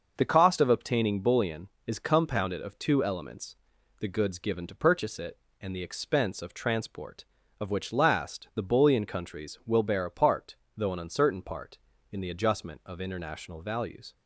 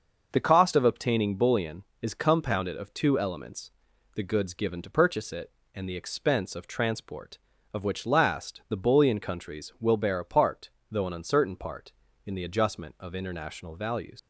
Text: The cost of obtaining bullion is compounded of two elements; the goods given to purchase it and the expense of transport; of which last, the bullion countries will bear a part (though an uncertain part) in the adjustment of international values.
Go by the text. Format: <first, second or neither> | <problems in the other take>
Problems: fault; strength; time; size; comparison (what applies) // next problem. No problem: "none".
first | starts louder than the rest; noticeable; until 1.3 s; 6 dB; noticeable in the first // leaves "values" unfinished; at 14.1 s; 90 ms